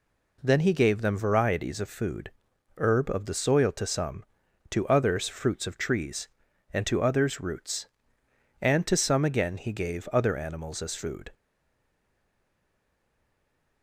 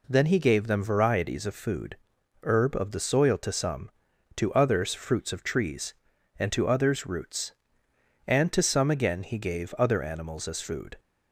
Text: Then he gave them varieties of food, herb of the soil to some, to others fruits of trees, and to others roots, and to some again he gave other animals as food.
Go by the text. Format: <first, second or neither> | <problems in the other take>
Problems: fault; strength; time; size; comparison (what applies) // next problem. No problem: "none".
second | stays silent after the last word; from 11.3 s on; 2.5 s long